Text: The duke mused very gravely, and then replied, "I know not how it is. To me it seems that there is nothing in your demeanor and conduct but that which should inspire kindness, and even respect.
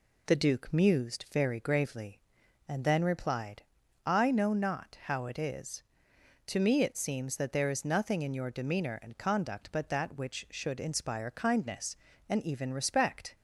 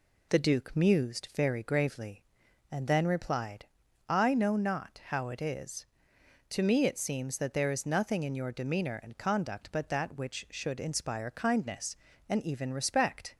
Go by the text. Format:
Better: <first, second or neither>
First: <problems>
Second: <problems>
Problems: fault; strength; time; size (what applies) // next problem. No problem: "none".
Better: neither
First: none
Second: none